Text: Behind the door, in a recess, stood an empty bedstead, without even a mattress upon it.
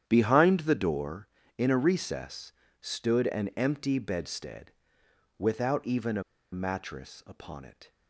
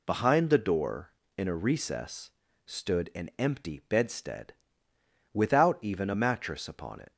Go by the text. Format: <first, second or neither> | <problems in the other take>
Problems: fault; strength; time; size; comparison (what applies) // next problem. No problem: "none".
second | starts louder than the rest; strong; until 1.0 s; 9.5 dB // pauses between "a" and "mattress"; slight; at 6.2 s; 0.29 s long